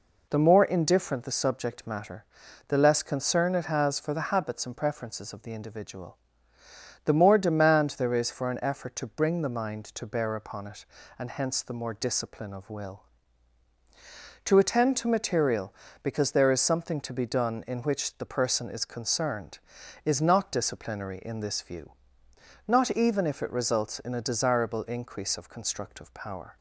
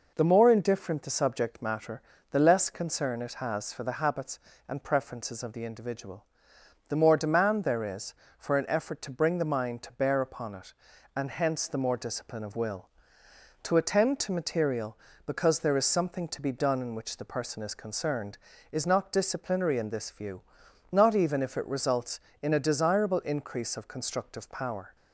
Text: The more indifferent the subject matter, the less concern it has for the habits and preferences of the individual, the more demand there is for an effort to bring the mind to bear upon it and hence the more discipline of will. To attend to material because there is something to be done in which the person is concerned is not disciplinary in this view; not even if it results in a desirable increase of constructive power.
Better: neither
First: none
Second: none

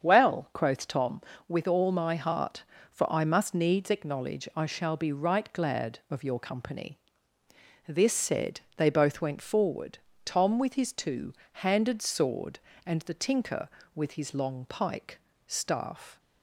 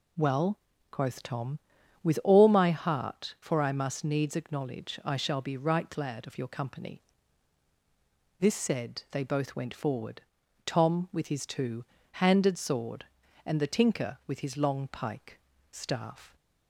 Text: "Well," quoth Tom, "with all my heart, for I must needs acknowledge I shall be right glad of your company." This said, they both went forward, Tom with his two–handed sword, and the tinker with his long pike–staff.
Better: second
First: starts louder than the rest; strong; until 1.0 s; 7.5 dB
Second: none

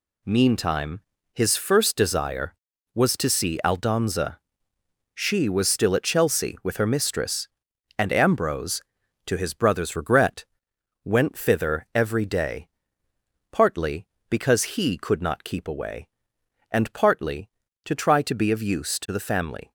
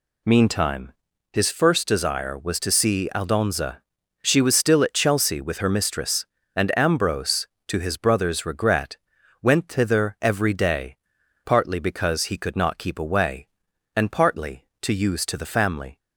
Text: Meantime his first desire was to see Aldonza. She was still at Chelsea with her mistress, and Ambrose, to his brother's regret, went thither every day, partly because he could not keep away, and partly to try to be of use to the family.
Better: first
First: pauses between "Meantime" and "his"; slight; at 1.0 s; 0.34 s long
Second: pauses between "Meantime" and "his"; at 0.9 s; 0.42 s long // skips "try to be of"; at 14.9 s

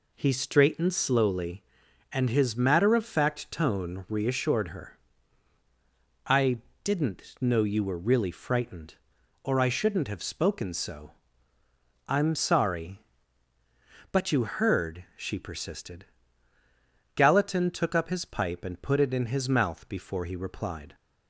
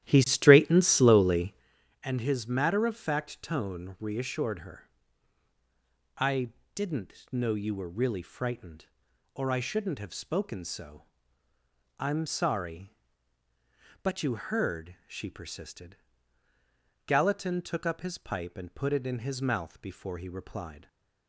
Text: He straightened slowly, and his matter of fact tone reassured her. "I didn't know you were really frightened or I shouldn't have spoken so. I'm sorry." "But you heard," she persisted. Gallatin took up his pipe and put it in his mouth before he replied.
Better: first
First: pauses between "I" and "didn't"; slight; at 6.6 s; 0.22 s long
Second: starts louder than the rest; strong; until 1.7 s; 12.5 dB // pauses between "I" and "didn't"; slight; at 6.5 s; 0.22 s long // stays silent after the last word; slight; from 20.7 s on; 0.5 s long

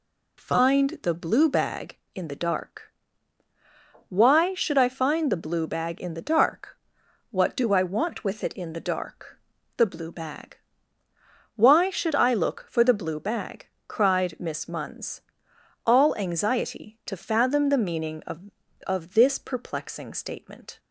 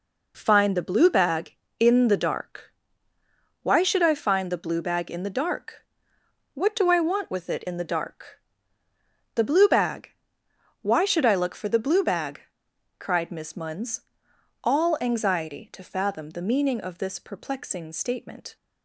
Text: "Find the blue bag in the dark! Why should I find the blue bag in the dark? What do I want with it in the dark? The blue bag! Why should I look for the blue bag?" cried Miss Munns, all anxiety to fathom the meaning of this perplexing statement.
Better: second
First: says "of" twice; at 18.8 s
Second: none

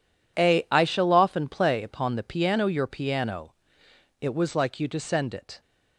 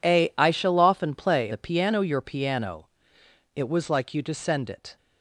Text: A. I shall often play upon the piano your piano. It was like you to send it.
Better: first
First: none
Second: skips "upon"; at 1.5 s

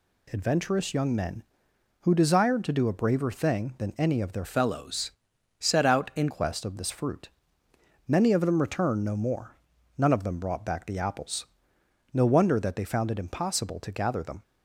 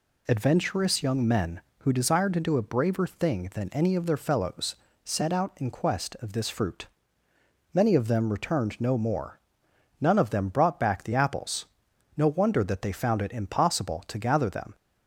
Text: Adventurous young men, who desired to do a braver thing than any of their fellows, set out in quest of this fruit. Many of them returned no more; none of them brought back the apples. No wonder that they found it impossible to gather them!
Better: second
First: changes voice from "fellows" to "in"; from 4.4 to 6.2 s; 1.8 s long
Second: none

